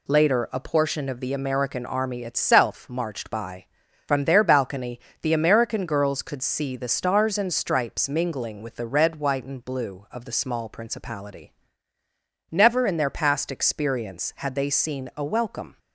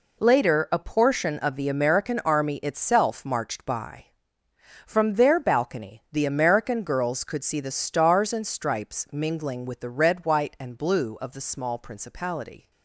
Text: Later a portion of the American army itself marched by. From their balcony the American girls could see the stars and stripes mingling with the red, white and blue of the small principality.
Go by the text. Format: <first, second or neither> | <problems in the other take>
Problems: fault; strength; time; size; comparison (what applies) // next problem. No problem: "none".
second | pauses between "balcony" and "the"; slight; at 5.0 s; 0.20 s long // goes on to say "Never in their past experience had they seen a welcome"; strong; from 12.5 s on; 3.2 s long